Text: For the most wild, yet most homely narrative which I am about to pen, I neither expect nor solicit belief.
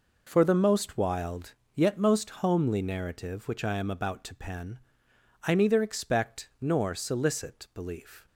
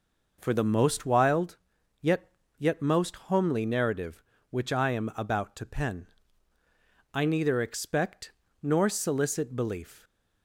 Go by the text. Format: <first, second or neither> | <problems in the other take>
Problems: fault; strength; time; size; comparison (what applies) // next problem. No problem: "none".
first | says "yet" twice; at 2.5 s // pauses between "expect" and "nor"; slight; at 8.3 s; 0.30 s long